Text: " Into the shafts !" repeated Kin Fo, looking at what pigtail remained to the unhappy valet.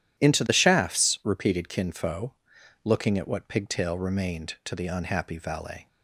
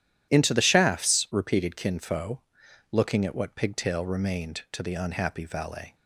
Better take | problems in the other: neither | starts louder than the rest; strong; the same in both

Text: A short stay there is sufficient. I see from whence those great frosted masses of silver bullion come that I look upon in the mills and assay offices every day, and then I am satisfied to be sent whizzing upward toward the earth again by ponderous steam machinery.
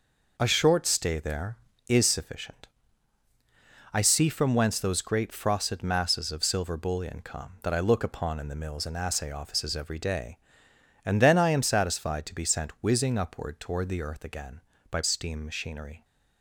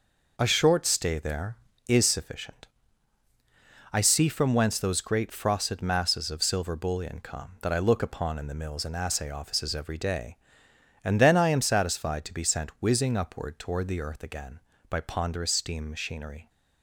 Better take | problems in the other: second | skips "ponderous"; at 15.0 s

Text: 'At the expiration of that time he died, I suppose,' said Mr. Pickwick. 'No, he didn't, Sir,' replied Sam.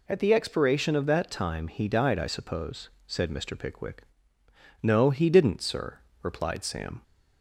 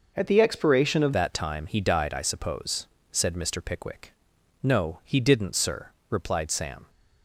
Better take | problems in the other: first | changes voice at "that"; from 1.1 s on; 5.7 s long

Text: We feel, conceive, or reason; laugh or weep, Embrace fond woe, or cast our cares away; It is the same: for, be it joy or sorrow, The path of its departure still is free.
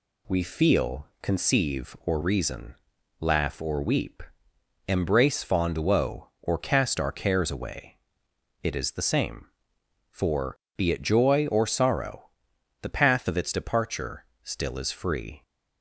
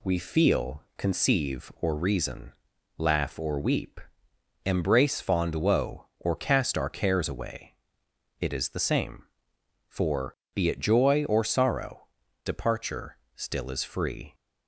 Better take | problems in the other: first | skips "The path of its"; at 12.2 s // pauses between "departure" and "still"; slight; at 13.1 s; 0.18 s long; slight in the first

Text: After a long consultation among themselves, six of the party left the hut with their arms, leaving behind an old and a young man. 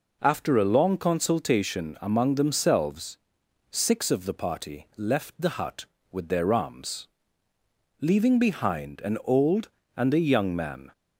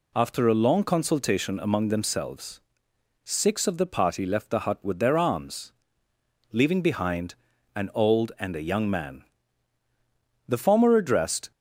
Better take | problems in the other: first | pauses between "behind" and "an"; at 7.3 s; 0.40 s long // goes on to say "The former addressed"; noticeable; from 10.4 s on; 1.0 s long

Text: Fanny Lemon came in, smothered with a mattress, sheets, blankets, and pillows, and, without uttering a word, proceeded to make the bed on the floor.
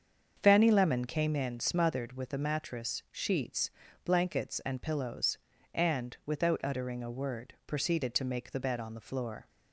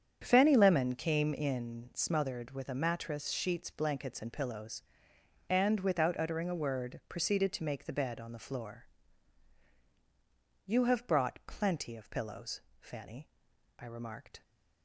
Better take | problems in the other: first | starts louder than the rest; strong; until 1.2 s; 8 dB; also in the first // goes on to say "You have brought plenty of pillows Fanny I remarked"; strong; from 10.6 s on; 3.7 s long

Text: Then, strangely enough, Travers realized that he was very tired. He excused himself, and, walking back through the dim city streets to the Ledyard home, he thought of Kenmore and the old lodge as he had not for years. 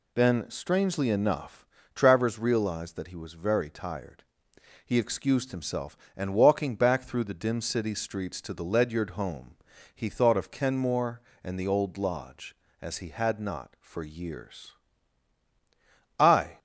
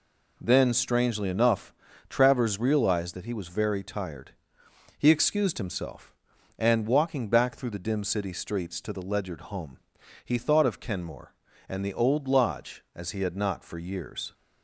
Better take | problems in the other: second | goes on to say "I"; slight; from 16.1 s on; 0.40 s long

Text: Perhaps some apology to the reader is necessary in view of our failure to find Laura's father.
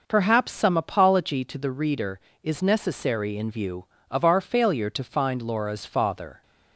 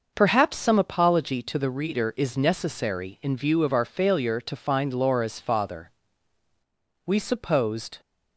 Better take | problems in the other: first | starts louder than the rest; noticeable; until 1.1 s; 6 dB // goes on to say "We supposed"; noticeable; from 7.0 s on; 0.94 s long

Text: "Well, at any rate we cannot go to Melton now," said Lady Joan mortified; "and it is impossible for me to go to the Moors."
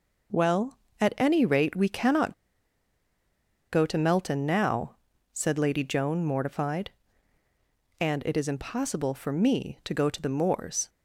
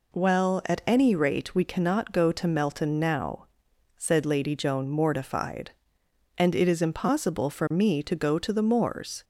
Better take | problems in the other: second | pauses between "cannot" and "go"; strong; at 2.3 s; 1.3 s long

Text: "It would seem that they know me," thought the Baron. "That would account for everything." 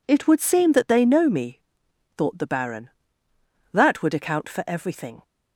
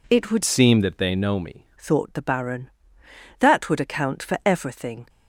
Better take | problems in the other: first | changes voice from "seem" to "me"; from 0.4 to 1.6 s; 1.2 s long

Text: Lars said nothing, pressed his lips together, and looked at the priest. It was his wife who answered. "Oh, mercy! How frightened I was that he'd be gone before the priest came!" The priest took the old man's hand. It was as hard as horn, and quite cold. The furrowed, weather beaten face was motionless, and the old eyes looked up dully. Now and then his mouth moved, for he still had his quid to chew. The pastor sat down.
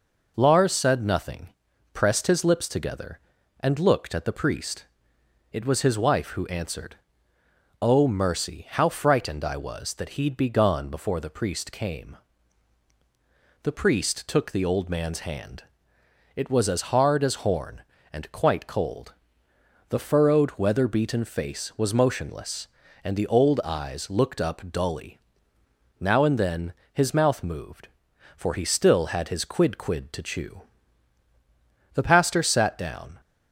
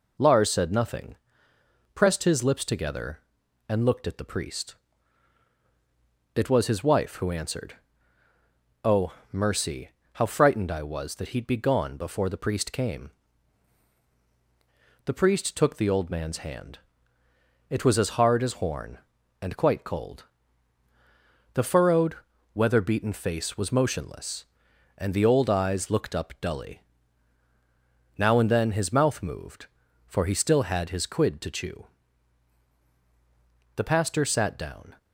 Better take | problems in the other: second | pauses between "then" and "his"; slight; at 26.7 s; 0.20 s long // says "quid" twice; at 29.7 s

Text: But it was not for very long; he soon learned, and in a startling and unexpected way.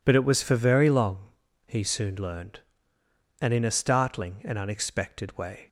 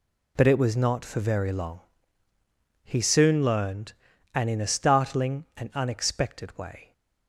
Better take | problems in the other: second | skips "not"; at 0.4 s

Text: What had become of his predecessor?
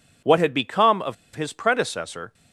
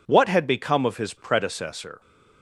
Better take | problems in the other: second | pauses between "of" and "his"; slight; at 1.1 s; 0.20 s long

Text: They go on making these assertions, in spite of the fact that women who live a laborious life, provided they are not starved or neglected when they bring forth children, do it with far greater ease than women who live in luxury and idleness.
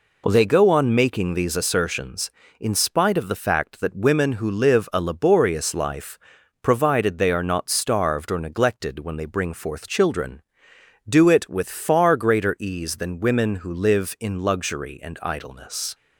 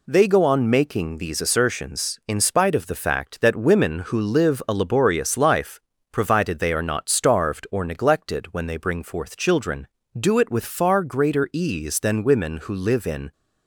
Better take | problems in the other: first | stops before "luxury and idleness"; at 13.3 s

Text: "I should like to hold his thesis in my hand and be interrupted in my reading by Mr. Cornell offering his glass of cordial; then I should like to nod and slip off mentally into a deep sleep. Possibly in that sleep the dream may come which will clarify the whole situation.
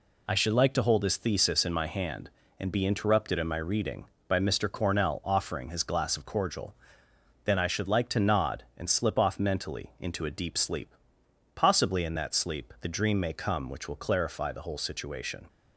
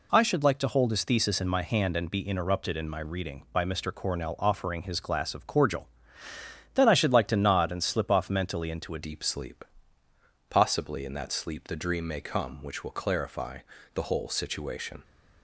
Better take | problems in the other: first | changes voice at "deep"; from 9.0 s on; 6.0 s long // pauses between "clarify" and "the"; slight; at 13.6 s; 0.32 s long

